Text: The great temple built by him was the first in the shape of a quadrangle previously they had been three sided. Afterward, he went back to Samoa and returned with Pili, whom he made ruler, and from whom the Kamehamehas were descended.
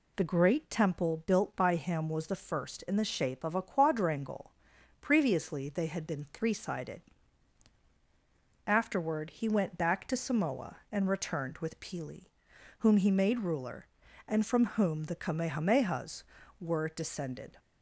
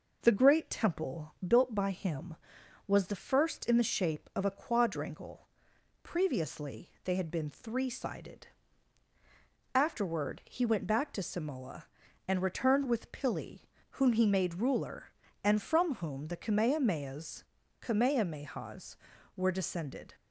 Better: first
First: pauses between "quadrangle" and "previously"; noticeable; at 4.5 s; 0.48 s long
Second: pauses between "quadrangle" and "previously"; noticeable; at 5.4 s; 0.56 s long // says "Kamehamehas" twice; at 17.8 s

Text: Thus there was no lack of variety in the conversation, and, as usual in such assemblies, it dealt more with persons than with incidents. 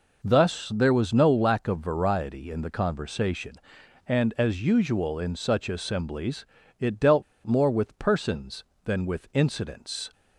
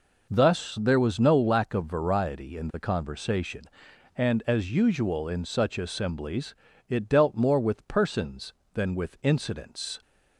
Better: second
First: pauses between "dealt" and "more"; slight; at 7.2 s; 0.22 s long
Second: none

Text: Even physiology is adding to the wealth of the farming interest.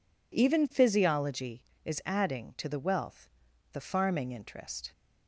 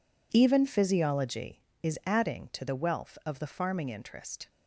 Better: second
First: skips "of"; at 3.5 s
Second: none

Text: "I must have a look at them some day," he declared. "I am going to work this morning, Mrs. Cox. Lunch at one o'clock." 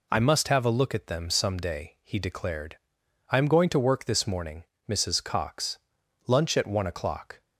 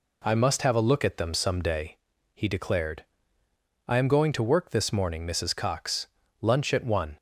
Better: first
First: none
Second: stops before "o'clock"; at 7.1 s

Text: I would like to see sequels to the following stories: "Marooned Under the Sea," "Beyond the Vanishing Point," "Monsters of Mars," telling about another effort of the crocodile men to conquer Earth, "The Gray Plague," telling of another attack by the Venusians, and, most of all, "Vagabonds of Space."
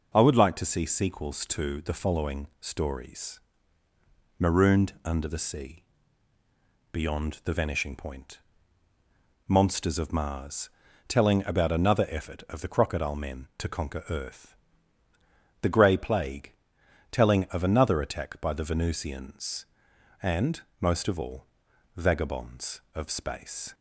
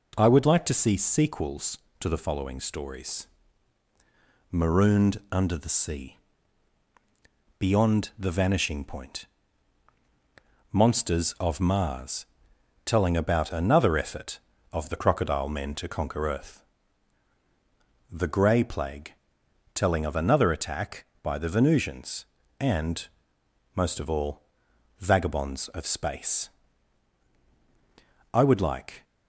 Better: first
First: none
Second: goes on to say "I would like"; noticeable; from 28.3 s on; 0.72 s long

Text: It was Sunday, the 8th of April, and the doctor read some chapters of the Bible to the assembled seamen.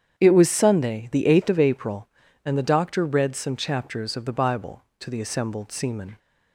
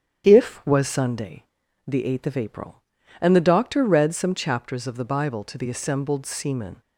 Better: first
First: starts louder than the rest; strong; until 1.1 s; 8.5 dB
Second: starts louder than the rest; strong; until 1.2 s; 9 dB // says "If" for "It"; at 0.2 s

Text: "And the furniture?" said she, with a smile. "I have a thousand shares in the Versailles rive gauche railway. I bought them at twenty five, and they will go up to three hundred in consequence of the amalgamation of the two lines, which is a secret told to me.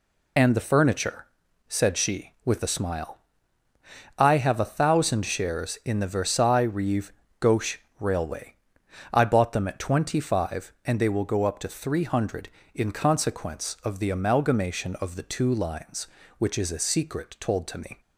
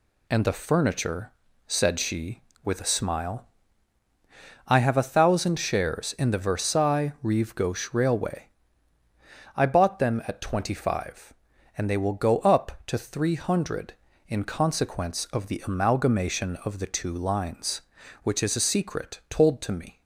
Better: second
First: loses the start of "And"; at 0.3 s; 40 ms // pauses between "rive" and "gauche"; slight; at 7.1 s; 0.28 s long // pauses between "gauche" and "railway"; slight; at 7.7 s; 0.20 s long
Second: none

